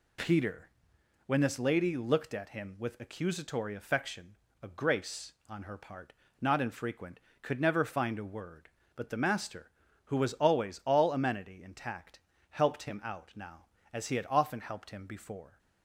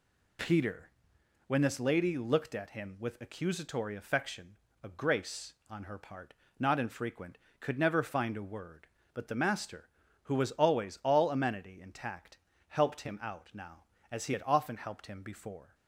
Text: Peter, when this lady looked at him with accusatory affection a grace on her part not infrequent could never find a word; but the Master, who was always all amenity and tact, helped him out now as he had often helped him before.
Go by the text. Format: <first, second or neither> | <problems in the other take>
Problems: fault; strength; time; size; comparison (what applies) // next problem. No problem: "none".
neither | pauses between "affection" and "a"; slight; the same in both // pauses between "part" and "not"; slight; the same in both